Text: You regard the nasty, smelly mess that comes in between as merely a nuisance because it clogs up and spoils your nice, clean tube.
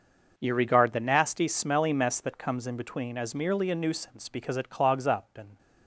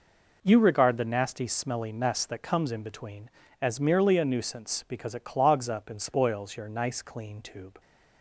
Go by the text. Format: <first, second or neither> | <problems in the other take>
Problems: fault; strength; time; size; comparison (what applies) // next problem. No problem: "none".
second | starts louder than the rest; noticeable; until 1.3 s; 6 dB // stops before "spoils your nice clean tube"; at 5.5 s